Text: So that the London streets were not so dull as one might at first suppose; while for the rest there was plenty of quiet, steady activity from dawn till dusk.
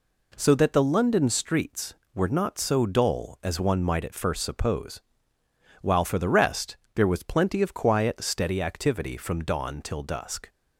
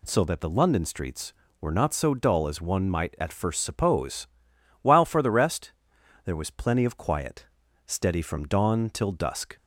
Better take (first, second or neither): first